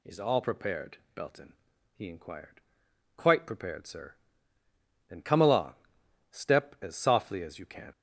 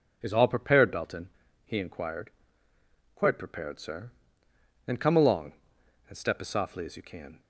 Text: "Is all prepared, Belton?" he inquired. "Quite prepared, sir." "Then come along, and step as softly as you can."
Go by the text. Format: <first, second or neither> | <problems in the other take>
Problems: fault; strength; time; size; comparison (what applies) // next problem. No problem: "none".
second | skips "and"; at 6.0 s